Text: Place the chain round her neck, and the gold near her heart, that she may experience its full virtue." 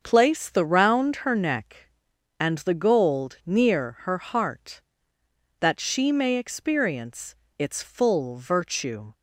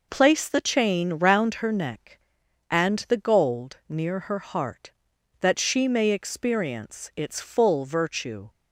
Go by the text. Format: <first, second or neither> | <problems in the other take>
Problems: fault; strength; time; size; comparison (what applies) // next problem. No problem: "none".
second | starts louder than the rest; until 1.0 s; 7 dB // skips "chain"; at 0.6 s // pauses between "experience" and "its"; slight; at 7.3 s; 0.24 s long